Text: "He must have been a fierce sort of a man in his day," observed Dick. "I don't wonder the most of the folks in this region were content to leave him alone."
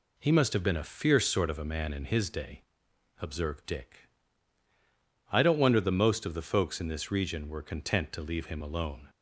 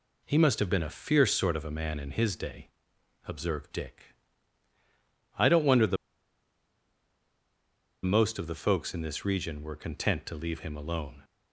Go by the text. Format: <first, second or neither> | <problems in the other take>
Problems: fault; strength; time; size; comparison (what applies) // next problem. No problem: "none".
first | pauses between "the" and "most"; strong; at 5.9 s; 2.0 s long